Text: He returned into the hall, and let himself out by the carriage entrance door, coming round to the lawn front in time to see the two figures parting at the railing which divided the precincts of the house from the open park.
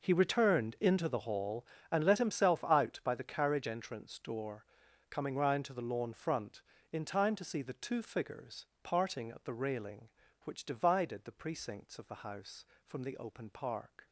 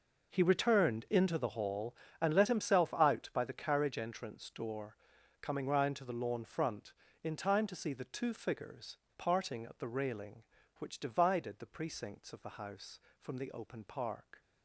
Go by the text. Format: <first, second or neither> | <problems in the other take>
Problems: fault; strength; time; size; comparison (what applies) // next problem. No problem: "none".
neither | pauses between "figures" and "parting"; slight; the same in both